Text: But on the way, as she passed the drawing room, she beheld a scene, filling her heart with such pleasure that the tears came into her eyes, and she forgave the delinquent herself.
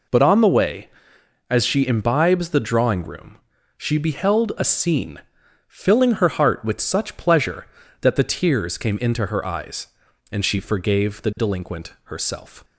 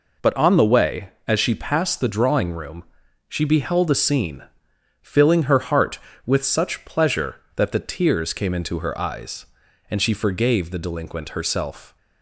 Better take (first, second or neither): second